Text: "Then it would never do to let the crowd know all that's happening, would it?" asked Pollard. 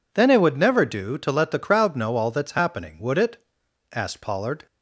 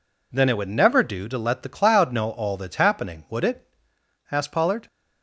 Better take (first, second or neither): first